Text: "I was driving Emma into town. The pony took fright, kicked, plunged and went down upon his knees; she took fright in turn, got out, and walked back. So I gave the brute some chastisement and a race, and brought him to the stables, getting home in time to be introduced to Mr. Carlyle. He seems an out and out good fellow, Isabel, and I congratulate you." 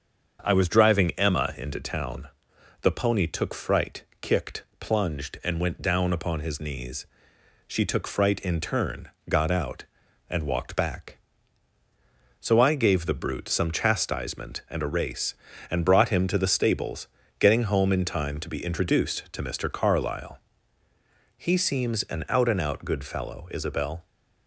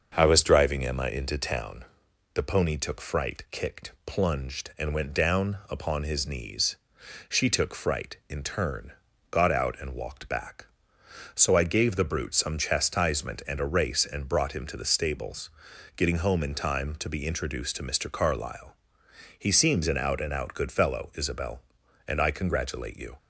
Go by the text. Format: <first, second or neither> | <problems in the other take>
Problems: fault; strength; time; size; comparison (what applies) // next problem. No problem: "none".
second | starts louder than the rest; until 1.4 s; 7 dB; also in the second // stops before "and I congratulate you"; at 24.0 s